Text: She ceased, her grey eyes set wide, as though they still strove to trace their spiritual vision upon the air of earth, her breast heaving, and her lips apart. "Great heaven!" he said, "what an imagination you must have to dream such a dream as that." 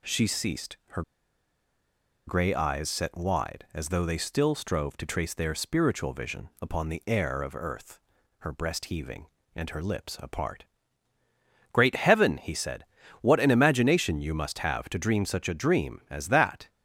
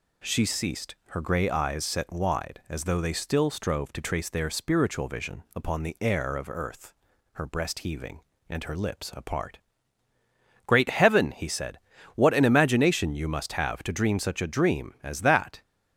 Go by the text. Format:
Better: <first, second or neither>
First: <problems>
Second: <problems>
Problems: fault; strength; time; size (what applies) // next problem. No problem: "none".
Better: second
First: pauses between "her" and "grey"; strong; at 1.0 s; 1.2 s long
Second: none